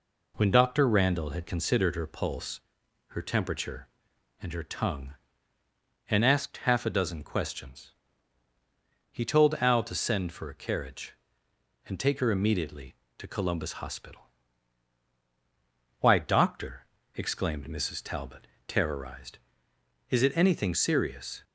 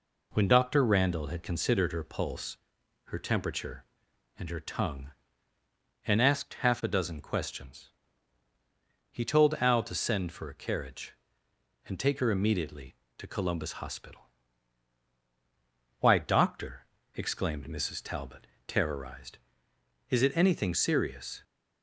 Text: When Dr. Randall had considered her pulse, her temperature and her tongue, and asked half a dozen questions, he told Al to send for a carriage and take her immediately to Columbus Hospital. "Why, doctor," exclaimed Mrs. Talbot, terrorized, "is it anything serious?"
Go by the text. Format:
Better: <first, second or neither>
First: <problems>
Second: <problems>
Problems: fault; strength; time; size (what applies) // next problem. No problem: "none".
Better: neither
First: none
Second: none